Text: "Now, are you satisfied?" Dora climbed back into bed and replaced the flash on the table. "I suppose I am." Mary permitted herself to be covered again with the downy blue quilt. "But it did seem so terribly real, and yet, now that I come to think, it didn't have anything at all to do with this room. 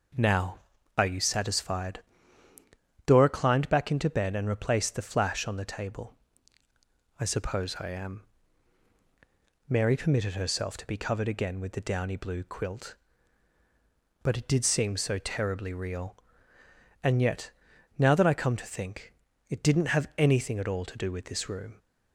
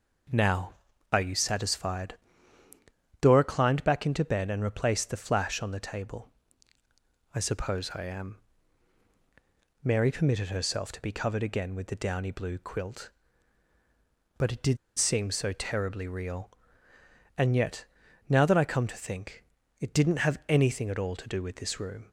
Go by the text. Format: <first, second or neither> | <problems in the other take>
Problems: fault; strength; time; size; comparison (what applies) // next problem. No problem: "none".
first | pauses between "did" and "seem"; slight; at 14.7 s; 0.20 s long